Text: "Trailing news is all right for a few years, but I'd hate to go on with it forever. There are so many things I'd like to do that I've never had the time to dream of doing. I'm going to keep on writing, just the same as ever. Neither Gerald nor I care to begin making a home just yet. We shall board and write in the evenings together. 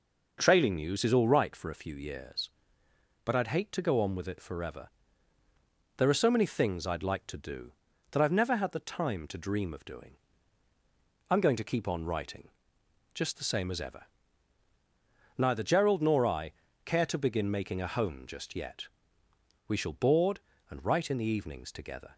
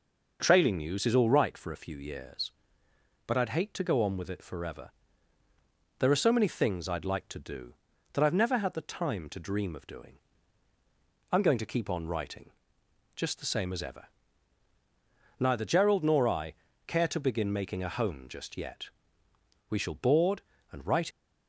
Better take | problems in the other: first | pauses between "I" and "care"; slight; at 16.5 s; 0.32 s long; slight in the first // stops before "in the evenings together"; at 21.1 s

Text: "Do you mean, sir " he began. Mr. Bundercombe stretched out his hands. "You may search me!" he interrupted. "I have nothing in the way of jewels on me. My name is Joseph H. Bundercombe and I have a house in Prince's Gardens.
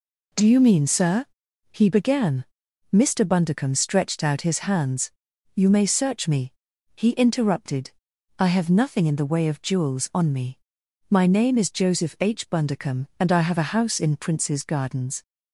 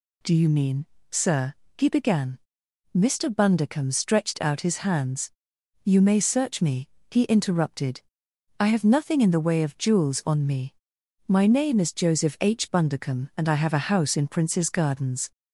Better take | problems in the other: first | gets louder; slight; throughout; 2.5 dB

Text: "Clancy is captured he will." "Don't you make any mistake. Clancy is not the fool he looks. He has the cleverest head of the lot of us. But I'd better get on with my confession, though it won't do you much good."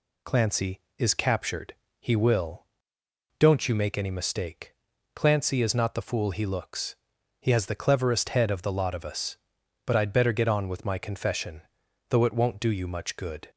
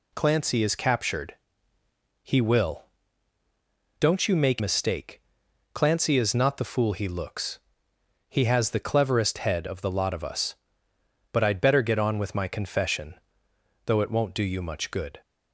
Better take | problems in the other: first | pauses between "captured" and "he"; noticeable; at 1.3 s; 0.88 s long; slight in the first // skips "any"; at 4.5 s

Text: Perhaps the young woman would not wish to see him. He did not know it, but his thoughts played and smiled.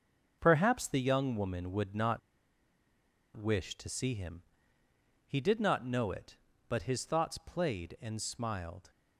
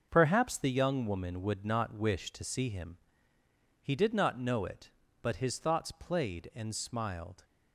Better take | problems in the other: second | starts louder than the rest; until 1.4 s; 6 dB; also in the second // pauses between "not" and "wish"; at 2.1 s; 1.1 s long

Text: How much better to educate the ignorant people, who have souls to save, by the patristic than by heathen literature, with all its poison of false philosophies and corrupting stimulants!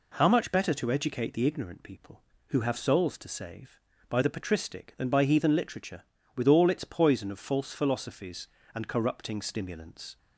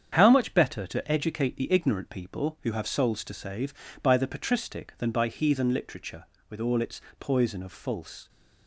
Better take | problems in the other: first | starts louder than the rest; strong; until 1.1 s; 8 dB // pauses between "its" and "poison"; slight; at 7.0 s; 0.18 s long // stops before "philosophies and corrupting stimulants"; at 8.2 s

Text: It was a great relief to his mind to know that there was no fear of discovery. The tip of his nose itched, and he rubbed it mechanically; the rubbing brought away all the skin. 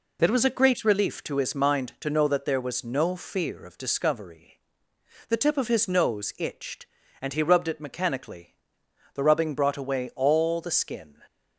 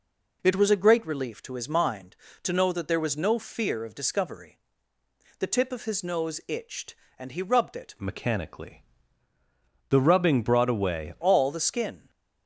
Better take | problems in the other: first | changes voice from "mechanically" to "away"; from 8.0 to 11.1 s; 3.1 s long

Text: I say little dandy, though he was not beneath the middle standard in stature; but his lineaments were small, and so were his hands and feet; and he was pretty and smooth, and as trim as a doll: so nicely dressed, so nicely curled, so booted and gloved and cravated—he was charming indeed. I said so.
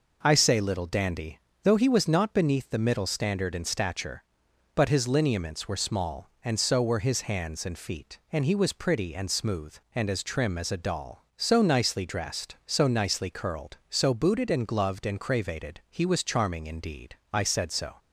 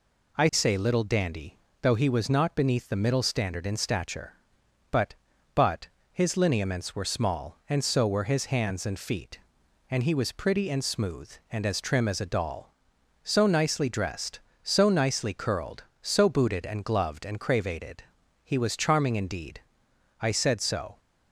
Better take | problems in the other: first | says "but" twice; at 5.5 s

